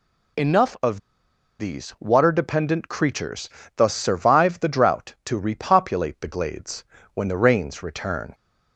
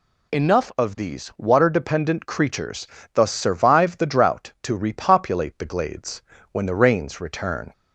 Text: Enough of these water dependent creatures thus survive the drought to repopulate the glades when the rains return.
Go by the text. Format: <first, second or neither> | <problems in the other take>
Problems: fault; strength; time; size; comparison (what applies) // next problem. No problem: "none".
second | pauses between "of" and "these"; noticeable; at 0.9 s; 0.60 s long // pauses between "creatures" and "thus"; slight; at 3.4 s; 0.28 s long; slight in the second // pauses between "glades" and "when"; slight; at 6.8 s; 0.32 s long; slight in the second